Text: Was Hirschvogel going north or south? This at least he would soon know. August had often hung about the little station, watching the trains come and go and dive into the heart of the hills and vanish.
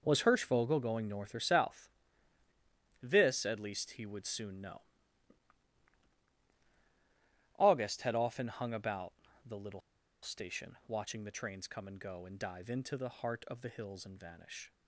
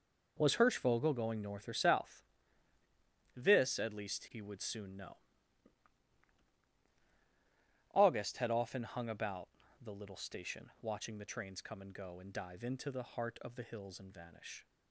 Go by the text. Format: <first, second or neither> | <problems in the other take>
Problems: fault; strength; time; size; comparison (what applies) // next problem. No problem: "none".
second | pauses between "about" and "the"; slight; at 9.1 s; 0.32 s long; slight in the second // pauses between "little" and "station"; at 9.7 s; 0.42 s long